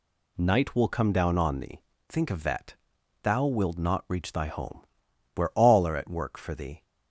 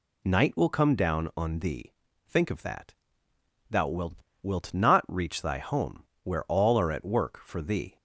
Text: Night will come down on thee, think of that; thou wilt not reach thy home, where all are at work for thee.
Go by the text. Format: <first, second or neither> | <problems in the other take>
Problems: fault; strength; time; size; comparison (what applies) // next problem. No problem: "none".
first | says "wilt" twice; at 4.4 s